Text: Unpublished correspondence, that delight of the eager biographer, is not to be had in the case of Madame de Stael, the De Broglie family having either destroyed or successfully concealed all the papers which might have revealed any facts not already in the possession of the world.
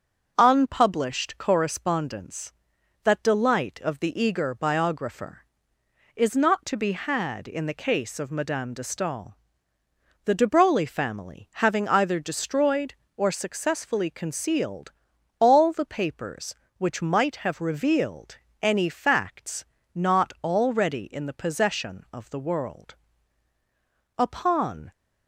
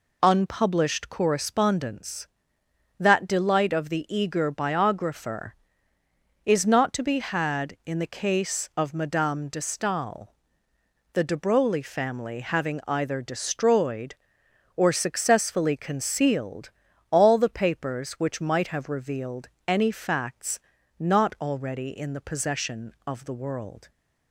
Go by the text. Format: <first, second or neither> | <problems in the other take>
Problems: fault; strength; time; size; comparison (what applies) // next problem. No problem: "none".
second | starts louder than the rest; until 1.3 s; 7 dB // pauses between "concealed" and "all"; noticeable; at 14.9 s; 0.48 s long; also in the second // pauses between "revealed" and "any"; slight; at 18.3 s; 0.26 s long; slight in the second // pauses between "facts" and "not"; slight; at 19.6 s; 0.30 s long; also in the second // goes on to say "Upon"; noticeable; from 24.1 s on; 0.74 s long